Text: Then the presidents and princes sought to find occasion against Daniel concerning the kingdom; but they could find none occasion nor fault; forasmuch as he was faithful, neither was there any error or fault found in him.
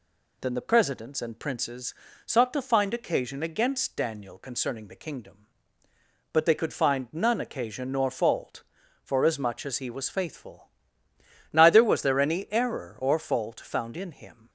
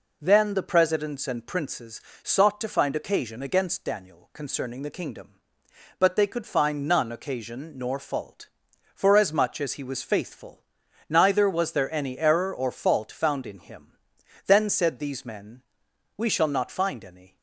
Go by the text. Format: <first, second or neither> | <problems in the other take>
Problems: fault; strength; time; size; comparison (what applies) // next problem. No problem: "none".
first | pauses between "princes" and "sought"; slight; at 2.0 s; 0.22 s long; slight in the first // goes on to say "Then said these men We shall not find any"; strong; from 14.4 s on; 2.9 s long